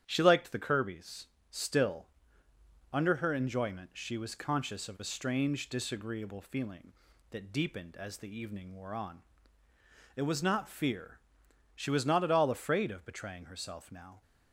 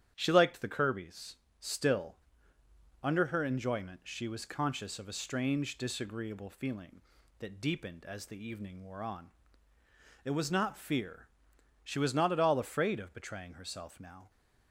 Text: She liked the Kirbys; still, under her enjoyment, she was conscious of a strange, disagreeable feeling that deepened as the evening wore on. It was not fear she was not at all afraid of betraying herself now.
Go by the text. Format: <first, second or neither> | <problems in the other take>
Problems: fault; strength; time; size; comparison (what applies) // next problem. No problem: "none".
neither | starts louder than the rest; strong; the same in both // pauses between "fear" and "she"; noticeable; the same in both